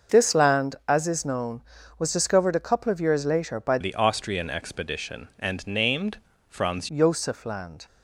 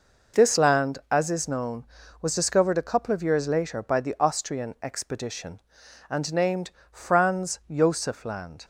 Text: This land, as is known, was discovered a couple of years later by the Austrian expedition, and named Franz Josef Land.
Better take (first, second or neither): second